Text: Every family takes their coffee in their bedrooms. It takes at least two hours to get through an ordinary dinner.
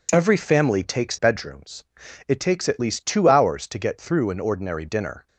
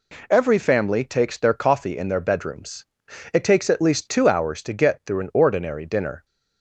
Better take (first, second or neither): second